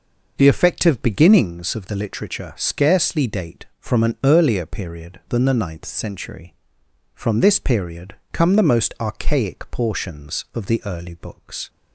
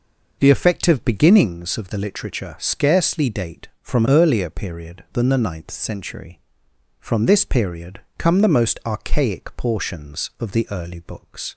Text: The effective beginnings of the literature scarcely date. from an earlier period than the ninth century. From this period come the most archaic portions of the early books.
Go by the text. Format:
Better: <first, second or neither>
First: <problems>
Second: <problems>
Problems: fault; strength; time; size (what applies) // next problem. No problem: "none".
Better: first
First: pauses between "period" and "come"; slight; at 8.1 s; 0.18 s long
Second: skips "an"; at 4.0 s // pauses between "period" and "come"; slight; at 8.0 s; 0.18 s long